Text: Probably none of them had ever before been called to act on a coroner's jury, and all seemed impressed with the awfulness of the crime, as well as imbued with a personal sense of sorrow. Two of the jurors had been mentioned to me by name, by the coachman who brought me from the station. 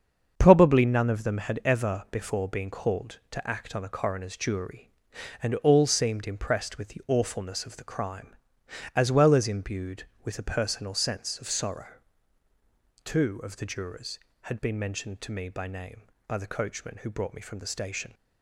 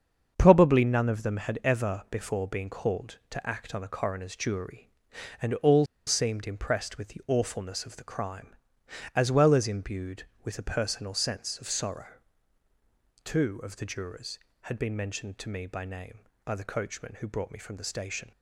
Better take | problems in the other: first | starts louder than the rest; until 1.3 s; 7 dB; also in the first // pauses between "all" and "seemed"; slight; at 5.8 s; 0.22 s long

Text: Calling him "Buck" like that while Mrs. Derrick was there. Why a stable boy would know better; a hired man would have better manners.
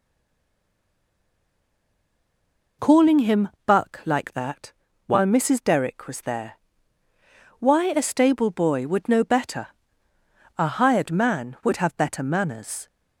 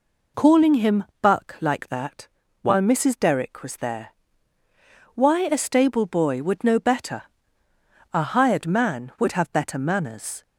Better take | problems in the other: second | stays silent before the first word; strong; until 2.7 s; 2.7 s long // pauses between "him" and "Buck"; slight; at 3.4 s; 0.16 s long; slight in the second // pauses between "that" and "while"; slight; at 4.7 s; 0.34 s long; slight in the second

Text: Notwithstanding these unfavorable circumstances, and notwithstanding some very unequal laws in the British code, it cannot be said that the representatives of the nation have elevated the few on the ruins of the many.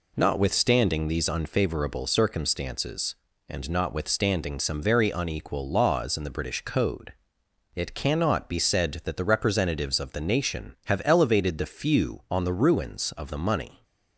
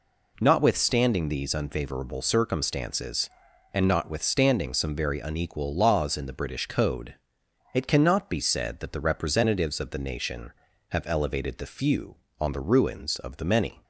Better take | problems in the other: second | says "money" for "many"; at 13.3 s

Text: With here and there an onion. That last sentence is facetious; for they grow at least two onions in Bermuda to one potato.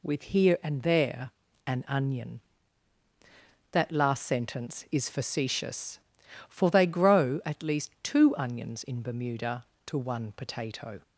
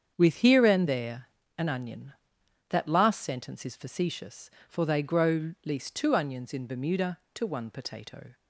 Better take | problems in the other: first | starts louder than the rest; strong; until 1.1 s; 7.5 dB // pauses between "there" and "an"; slight; at 1.2 s; 0.28 s long; also in the first // skips "at"; at 5.5 s

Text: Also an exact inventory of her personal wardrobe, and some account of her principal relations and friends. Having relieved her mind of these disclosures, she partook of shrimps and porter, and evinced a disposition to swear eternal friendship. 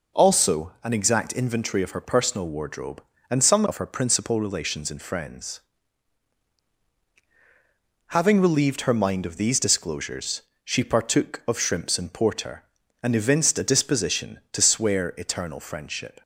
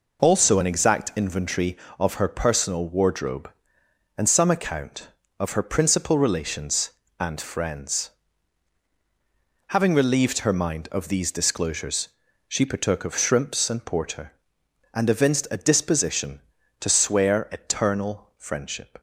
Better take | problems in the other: second | skips "account"; at 3.6 s

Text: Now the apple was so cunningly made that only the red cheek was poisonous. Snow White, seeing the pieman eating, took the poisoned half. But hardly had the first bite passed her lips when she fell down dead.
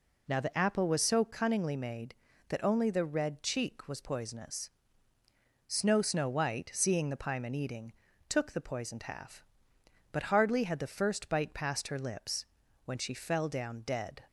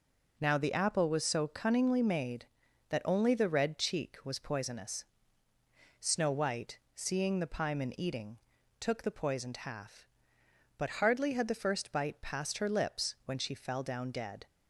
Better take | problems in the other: second | says "Snow" twice; at 6.0 s // pauses between "lips" and "when"; at 12.4 s; 0.40 s long

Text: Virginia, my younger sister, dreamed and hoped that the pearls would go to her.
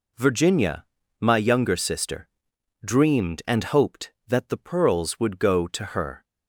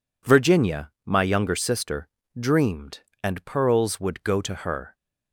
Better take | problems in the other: first | skips "hoped that the"; at 3.4 s

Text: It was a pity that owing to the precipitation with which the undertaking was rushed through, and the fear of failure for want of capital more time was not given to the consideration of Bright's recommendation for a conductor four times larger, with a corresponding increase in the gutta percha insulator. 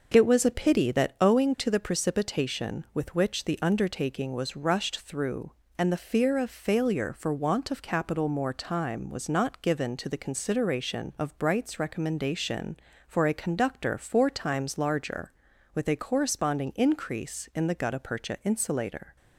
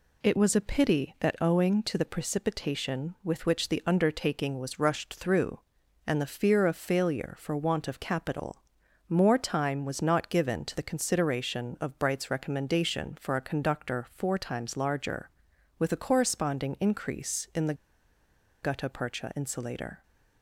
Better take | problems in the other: first | pauses between "capital" and "more"; noticeable; at 8.6 s; 0.46 s long // pauses between "the" and "gutta"; noticeable; at 17.7 s; 0.87 s long

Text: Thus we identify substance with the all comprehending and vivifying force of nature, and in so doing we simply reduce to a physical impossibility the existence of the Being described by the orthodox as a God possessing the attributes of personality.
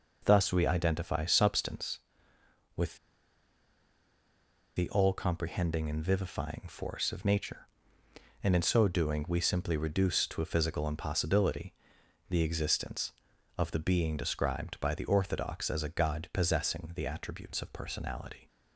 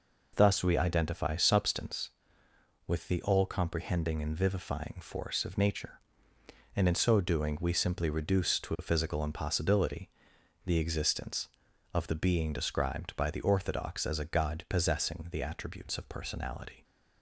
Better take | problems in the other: second | pauses between "with" and "the"; strong; at 2.9 s; 1.7 s long // pauses between "impossibility" and "the"; noticeable; at 11.7 s; 0.56 s long; noticeable in the second

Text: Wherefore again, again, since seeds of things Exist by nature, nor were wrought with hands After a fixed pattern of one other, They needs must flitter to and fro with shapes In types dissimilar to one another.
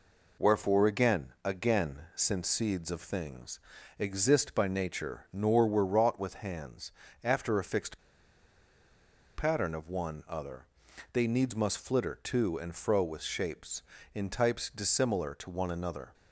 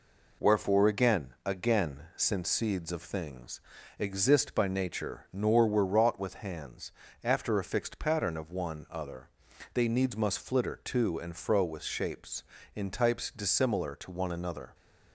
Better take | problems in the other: second | pauses between "things" and "Exist"; at 3.5 s; 0.40 s long; also in the second // pauses between "hands" and "After"; slight; at 6.9 s; 0.32 s long; slight in the second // pauses between "fixed" and "pattern"; strong; at 7.9 s; 1.3 s long

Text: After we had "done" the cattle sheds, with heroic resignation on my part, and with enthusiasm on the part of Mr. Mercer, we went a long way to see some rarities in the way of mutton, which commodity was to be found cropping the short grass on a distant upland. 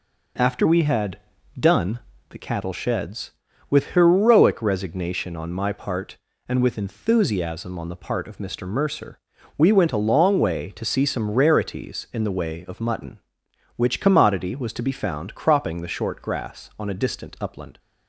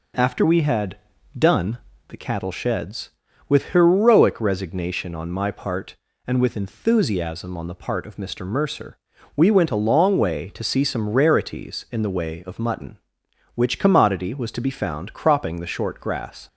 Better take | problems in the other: first | pauses between "had" and "done"; at 0.9 s; 0.42 s long; also in the first // pauses between "done" and "the"; slight; at 1.7 s; 0.30 s long; slight in the first // stops before "on a distant upland"; at 16.4 s

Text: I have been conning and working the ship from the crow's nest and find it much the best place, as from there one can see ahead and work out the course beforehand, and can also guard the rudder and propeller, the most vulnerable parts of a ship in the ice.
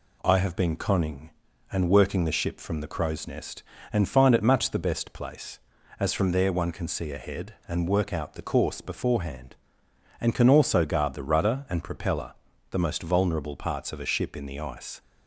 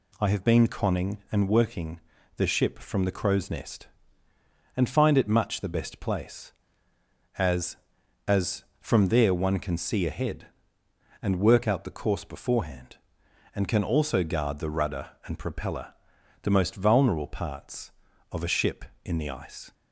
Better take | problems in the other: first | pauses between "working" and "the"; at 1.9 s; 0.38 s long // says "as" twice; at 8.2 s

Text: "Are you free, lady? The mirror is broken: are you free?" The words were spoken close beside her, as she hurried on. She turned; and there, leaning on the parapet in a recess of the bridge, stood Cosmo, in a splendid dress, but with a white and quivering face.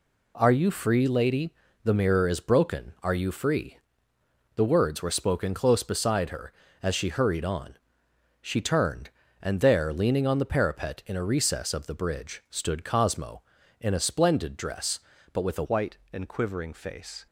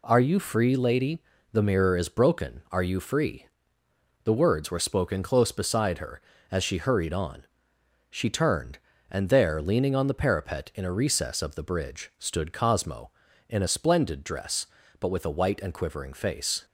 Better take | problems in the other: second | changes voice at "white"; from 15.6 s on; 1.6 s long

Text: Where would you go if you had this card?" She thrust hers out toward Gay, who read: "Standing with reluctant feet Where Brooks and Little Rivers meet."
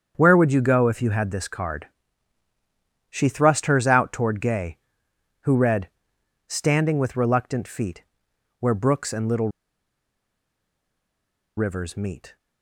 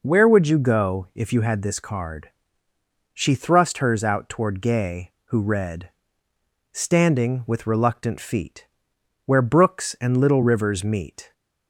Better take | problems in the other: second | starts louder than the rest; strong; until 1.1 s; 7 dB // pauses between "feet" and "Where"; noticeable; at 8.0 s; 0.58 s long; noticeable in the second // pauses between "Little" and "Rivers"; strong; at 9.4 s; 2.0 s long

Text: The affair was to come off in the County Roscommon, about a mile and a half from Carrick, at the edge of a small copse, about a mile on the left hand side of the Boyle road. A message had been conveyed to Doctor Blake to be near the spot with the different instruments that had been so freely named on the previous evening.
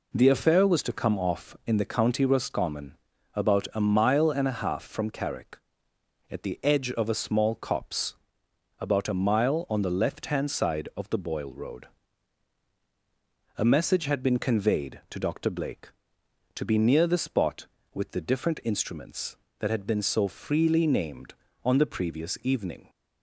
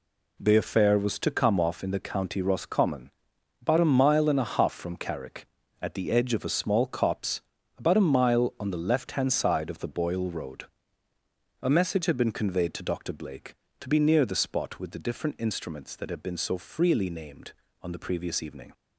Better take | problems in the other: neither | none

